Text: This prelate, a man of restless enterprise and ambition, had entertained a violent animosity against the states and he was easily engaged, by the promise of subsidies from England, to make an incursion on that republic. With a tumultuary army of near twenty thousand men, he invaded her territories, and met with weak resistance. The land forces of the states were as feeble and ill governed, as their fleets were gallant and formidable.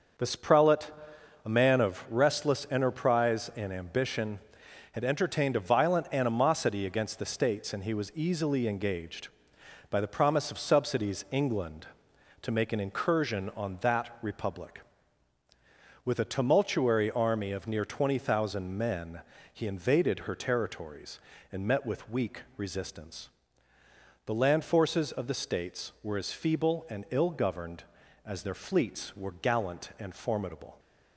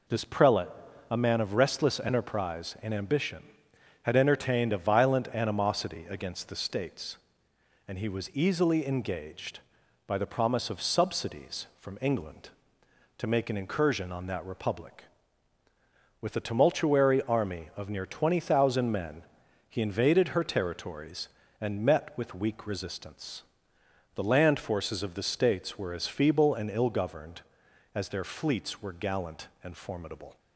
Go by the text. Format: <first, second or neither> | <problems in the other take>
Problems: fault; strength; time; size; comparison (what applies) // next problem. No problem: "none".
second | starts louder than the rest; until 1.7 s; 6 dB // skips "from"; at 11.2 s // pauses between "weak" and "resistance"; slight; at 22.4 s; 0.16 s long